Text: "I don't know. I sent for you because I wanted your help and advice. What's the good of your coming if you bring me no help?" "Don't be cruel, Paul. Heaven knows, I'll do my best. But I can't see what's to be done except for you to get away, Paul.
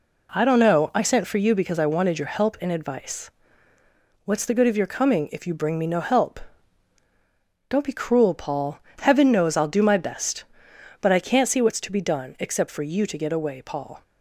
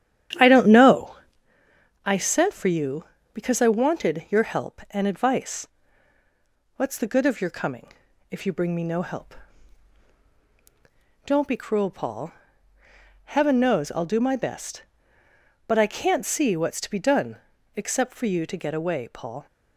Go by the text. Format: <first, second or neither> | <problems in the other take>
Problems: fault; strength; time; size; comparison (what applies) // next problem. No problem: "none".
first | starts louder than the rest; strong; until 1.4 s; 10 dB // pauses between "coming" and "if"; at 7.9 s; 0.38 s long // pauses between "done" and "except"; at 17.3 s; 0.38 s long